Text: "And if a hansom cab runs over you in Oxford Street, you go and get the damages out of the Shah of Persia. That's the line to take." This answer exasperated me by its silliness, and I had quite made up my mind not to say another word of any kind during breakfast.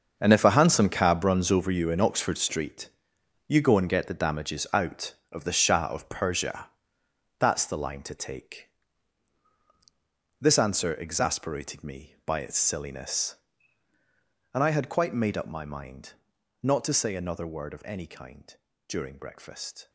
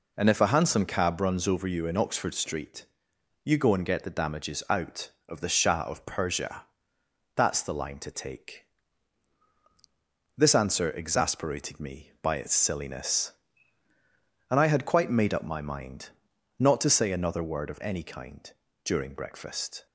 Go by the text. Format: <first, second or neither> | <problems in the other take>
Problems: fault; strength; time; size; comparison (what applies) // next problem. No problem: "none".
second | gets quieter; strong; throughout; 12.5 dB // pauses between "mind" and "not"; noticeable; at 16.1 s; 0.50 s long; noticeable in the second // pauses between "kind" and "during"; slight; at 18.5 s; 0.32 s long; slight in the second